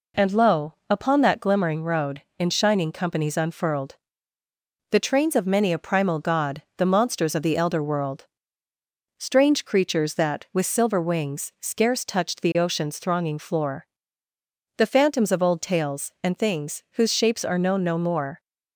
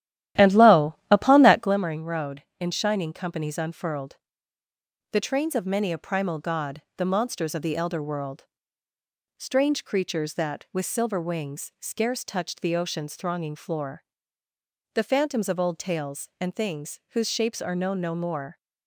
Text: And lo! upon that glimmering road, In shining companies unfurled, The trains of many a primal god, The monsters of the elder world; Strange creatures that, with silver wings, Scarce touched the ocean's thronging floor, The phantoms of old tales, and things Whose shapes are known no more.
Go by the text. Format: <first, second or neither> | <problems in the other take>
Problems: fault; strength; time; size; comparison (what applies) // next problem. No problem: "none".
first | starts louder than the rest; strong; until 1.8 s; 12.5 dB